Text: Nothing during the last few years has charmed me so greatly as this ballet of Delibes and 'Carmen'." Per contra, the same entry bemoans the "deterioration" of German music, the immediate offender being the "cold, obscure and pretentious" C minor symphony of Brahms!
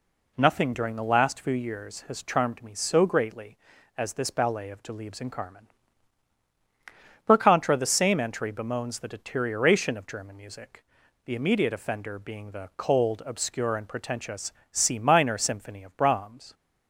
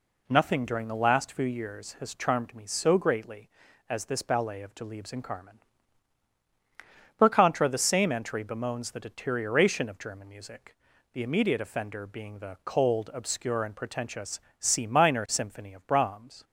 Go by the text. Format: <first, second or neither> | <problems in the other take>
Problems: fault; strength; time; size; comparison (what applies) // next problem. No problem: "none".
neither | pauses between "pretentious" and "C"; slight; the same in both